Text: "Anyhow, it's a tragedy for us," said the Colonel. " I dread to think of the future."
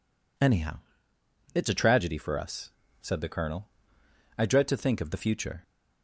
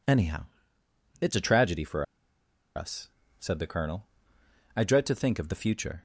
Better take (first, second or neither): first